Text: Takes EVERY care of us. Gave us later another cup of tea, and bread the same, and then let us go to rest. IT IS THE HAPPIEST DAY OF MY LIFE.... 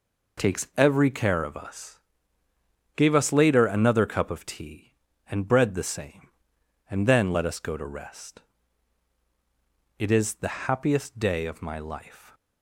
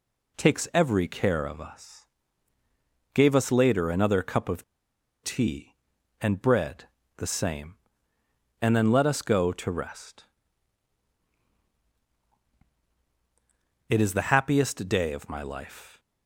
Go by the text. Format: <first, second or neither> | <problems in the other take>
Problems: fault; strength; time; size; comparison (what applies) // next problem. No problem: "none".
first | pauses between "of" and "tea"; noticeable; at 4.6 s; 0.59 s long // pauses between "bread" and "the"; slight; at 6.8 s; 0.32 s long